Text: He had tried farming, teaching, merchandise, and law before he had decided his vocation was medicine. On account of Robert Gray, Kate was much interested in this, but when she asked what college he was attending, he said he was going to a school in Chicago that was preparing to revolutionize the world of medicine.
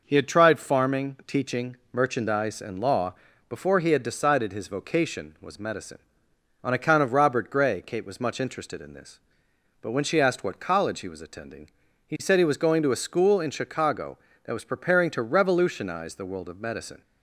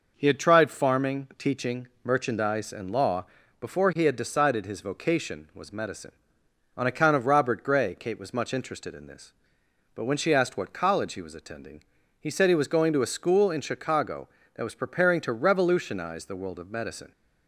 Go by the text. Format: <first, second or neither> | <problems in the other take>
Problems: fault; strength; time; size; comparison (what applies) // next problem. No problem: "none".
neither | pauses between "law" and "before"; slight; the same in both